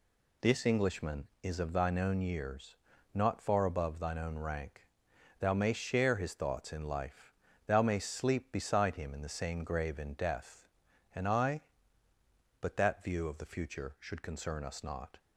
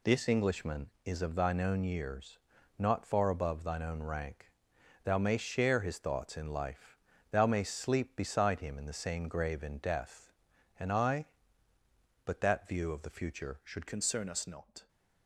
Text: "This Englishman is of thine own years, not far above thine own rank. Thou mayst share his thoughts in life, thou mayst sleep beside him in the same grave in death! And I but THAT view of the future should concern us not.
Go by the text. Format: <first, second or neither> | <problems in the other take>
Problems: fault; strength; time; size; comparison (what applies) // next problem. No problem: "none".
first | changes voice at "concern"; from 13.8 s on; 1.0 s long